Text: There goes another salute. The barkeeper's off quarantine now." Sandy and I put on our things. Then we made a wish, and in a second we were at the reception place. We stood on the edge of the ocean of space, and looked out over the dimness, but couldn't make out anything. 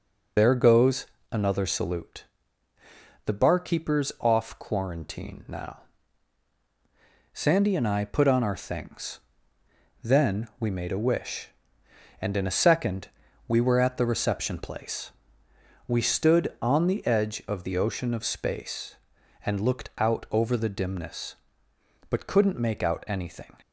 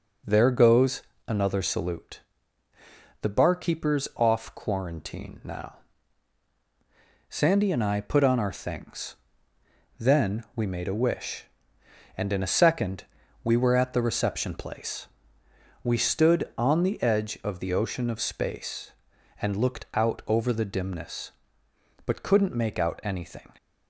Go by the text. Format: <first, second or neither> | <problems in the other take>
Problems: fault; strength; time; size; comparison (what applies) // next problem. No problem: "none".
second | loses the start of "There"; at 0.3 s; 85 ms // pauses between "goes" and "another"; slight; at 1.0 s; 0.26 s long; slight in the second // pauses between "second" and "we"; at 13.0 s; 0.38 s long; also in the second